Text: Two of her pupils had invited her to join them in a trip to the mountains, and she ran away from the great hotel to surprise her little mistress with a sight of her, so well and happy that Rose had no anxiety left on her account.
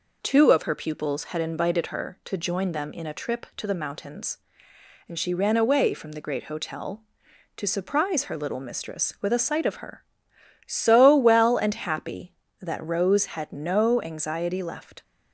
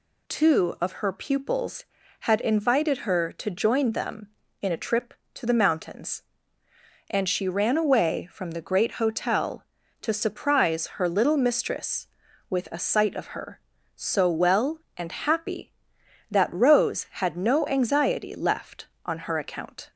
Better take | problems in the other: second | stops before "on her account"; at 15.0 s

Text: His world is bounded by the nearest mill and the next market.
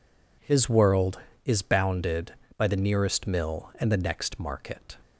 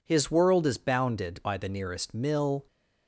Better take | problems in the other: first | stops before "and the next market"; at 2.6 s

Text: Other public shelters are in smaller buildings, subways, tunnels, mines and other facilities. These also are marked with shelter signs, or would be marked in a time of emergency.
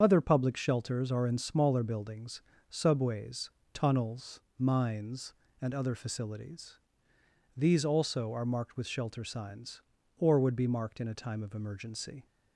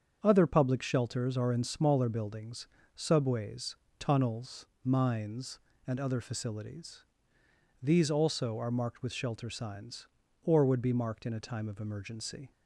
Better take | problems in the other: second | loses the start of "Other"; at 0.0 s; 35 ms // starts louder than the rest; strong; until 1.0 s; 7 dB; strong in the second

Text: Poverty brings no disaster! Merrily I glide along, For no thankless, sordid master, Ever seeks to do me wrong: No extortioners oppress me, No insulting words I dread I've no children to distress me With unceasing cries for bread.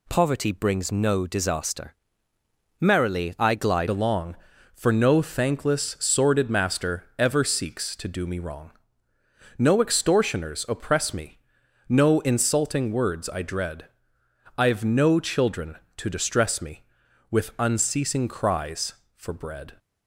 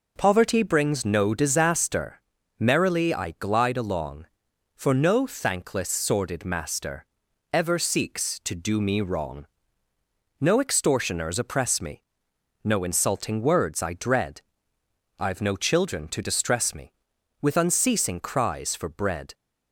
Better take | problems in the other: second | changes voice at "along"; from 3.8 s on; 15.9 s long // pauses between "dread" and "I've"; noticeable; at 13.8 s; 0.72 s long; noticeable in the second

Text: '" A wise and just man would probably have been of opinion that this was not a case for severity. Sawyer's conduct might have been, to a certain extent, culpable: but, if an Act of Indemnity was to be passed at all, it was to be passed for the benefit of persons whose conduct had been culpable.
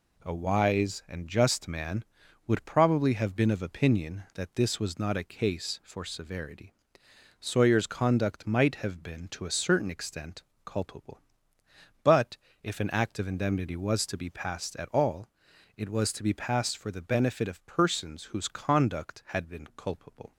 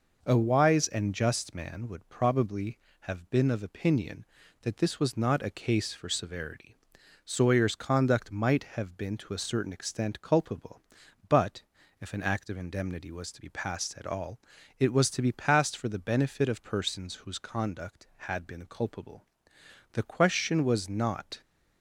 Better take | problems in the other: first | goes on to say "The question was not"; from 19.9 s on; 1.4 s long

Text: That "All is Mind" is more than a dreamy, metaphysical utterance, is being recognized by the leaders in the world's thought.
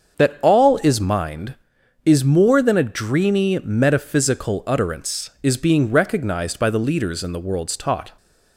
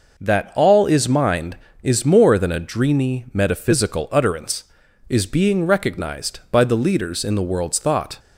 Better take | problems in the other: second | starts louder than the rest; until 1.2 s; 6.5 dB // says "taught" for "thought"; at 7.7 s

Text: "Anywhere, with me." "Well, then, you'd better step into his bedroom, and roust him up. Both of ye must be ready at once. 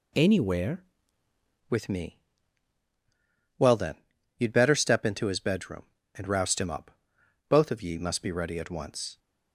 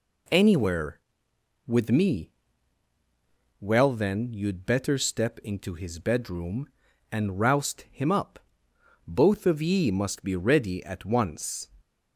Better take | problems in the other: second | changes voice at "with"; from 1.6 s on; 7.5 s long

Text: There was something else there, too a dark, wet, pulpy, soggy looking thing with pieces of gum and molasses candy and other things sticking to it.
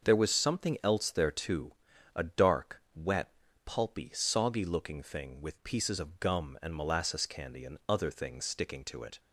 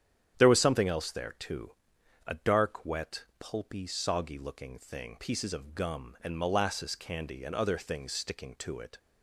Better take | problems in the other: first | starts louder than the rest; strong; until 1.4 s; 9.5 dB; also in the first // pauses between "too" and "a"; noticeable; at 1.7 s; 0.52 s long; also in the first // skips "with"; at 5.1 s

